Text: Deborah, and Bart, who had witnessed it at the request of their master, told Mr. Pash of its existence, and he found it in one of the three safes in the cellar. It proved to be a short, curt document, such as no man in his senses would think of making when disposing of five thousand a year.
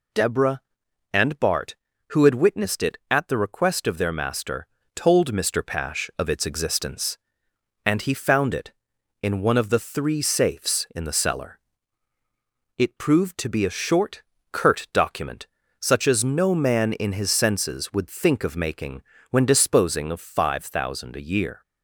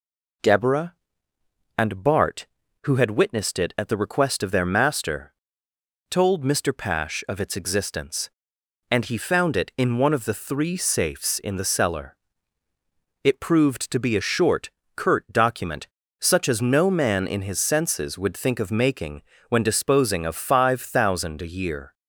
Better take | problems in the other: neither | pauses between "making" and "when"; slight; the same in both

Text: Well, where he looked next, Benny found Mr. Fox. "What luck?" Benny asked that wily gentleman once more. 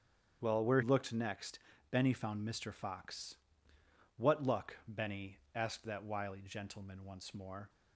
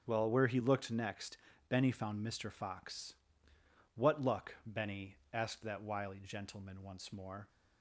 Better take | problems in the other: second | starts louder than the rest; strong; until 1.4 s; 8 dB; strong in the second // skips "he"; at 0.8 s // pauses between "Benny" and "asked"; slight; at 5.3 s; 0.18 s long; slight in the second

